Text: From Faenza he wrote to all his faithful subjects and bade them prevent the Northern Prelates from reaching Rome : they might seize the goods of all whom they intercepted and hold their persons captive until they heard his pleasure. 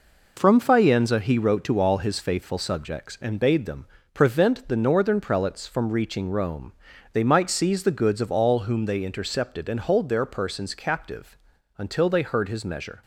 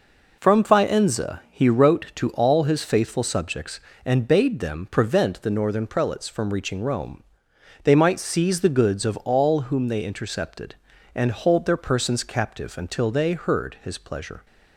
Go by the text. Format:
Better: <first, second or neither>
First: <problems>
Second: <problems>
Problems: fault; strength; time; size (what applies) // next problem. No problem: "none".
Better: second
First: pauses between "them" and "prevent"; slight; at 3.8 s; 0.28 s long // pauses between "captive" and "until"; at 11.3 s; 0.40 s long // says "measure" for "pleasure"; at 12.6 s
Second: none